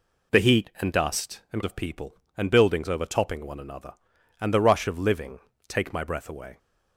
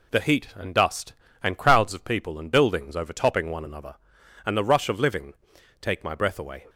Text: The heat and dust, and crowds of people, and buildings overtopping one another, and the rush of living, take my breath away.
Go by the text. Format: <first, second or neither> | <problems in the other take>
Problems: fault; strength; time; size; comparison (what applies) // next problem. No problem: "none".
second | skips "crowds"; at 1.6 s